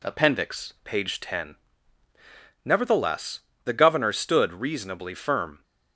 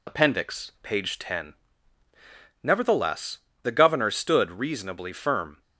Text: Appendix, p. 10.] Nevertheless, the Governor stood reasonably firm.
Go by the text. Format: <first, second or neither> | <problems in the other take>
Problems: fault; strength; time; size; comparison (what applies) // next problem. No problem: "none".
first | loses the start of "Appendix"; at 0.0 s; 70 ms